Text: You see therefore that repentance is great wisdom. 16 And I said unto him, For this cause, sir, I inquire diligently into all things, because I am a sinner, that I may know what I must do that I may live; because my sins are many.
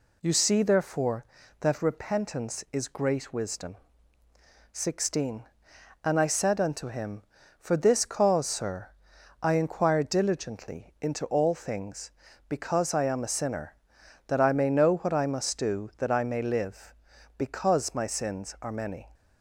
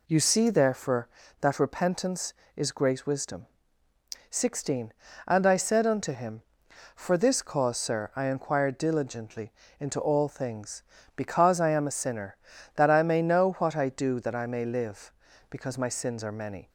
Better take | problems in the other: first | pauses between "diligently" and "into"; slight; at 9.5 s; 0.30 s long // skips "must"; at 13.8 s

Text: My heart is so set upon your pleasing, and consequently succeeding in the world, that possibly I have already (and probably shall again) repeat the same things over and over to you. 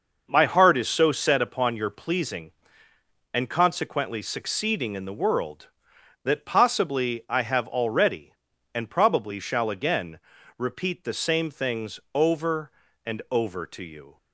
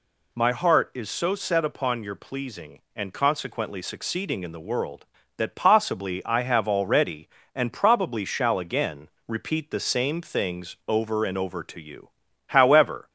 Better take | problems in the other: first | goes on to say "However"; noticeable; from 12.4 s on; 0.64 s long

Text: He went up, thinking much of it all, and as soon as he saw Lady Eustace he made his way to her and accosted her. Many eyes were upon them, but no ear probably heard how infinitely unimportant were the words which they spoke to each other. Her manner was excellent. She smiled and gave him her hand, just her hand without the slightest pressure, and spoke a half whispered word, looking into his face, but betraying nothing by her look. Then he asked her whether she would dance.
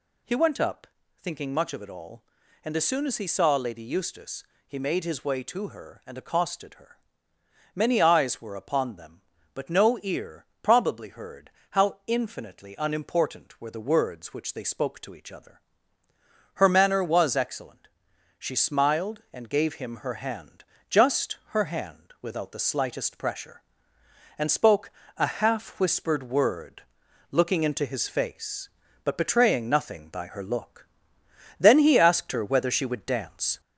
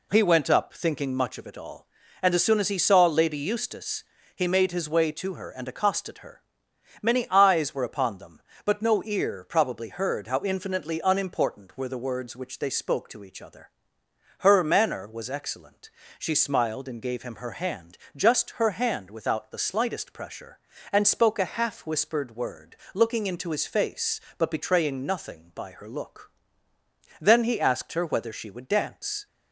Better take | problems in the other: second | gets louder; slight; throughout; 2.5 dB // pauses between "Eustace" and "he"; slight; at 4.4 s; 0.24 s long; slight in the second // pauses between "ear" and "probably"; slight; at 10.4 s; 0.20 s long // pauses between "heard" and "how"; slight; at 11.5 s; 0.20 s long // pauses between "spoke" and "a"; slight; at 24.9 s; 0.26 s long

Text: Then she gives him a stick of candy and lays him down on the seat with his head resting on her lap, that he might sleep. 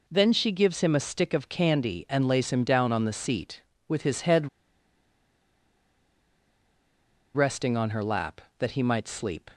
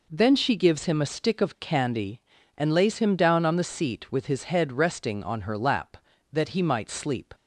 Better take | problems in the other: second | pauses between "head" and "resting"; strong; at 4.4 s; 2.8 s long

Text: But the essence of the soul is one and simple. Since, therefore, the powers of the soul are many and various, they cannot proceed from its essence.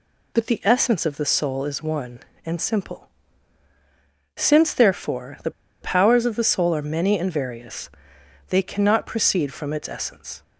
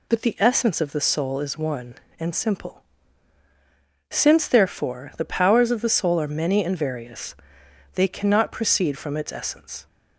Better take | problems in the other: second | pauses between "the" and "powers"; slight; at 5.5 s; 0.31 s long

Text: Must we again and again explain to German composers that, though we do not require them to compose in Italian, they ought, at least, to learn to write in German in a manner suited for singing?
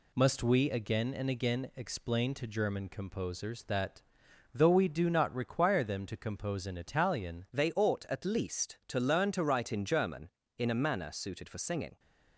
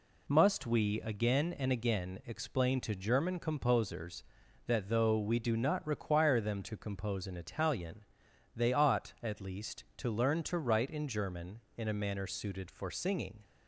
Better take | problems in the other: second | changes voice at "they"; from 7.5 s on; 4.4 s long

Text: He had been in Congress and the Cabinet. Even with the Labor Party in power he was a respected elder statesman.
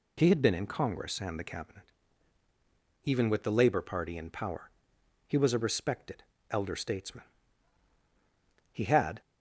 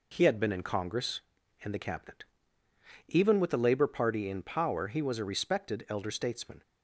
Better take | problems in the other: second | pauses between "power" and "he"; noticeable; at 4.6 s; 0.60 s long // pauses between "respected" and "elder"; slight; at 6.2 s; 0.26 s long // goes on to say "He had"; slight; from 8.7 s on; 0.48 s long

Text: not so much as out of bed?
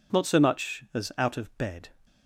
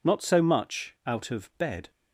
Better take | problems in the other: first | skips "as"; at 0.9 s

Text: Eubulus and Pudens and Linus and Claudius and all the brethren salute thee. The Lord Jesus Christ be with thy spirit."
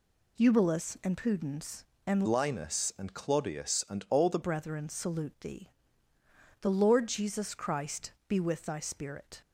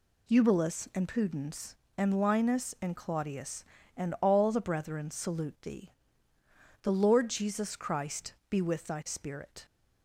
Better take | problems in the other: second | changes voice from "Linus" to "the"; from 2.2 to 4.3 s; 2.1 s long // pauses between "Christ" and "be"; slight; at 8.1 s; 0.16 s long; slight in the second

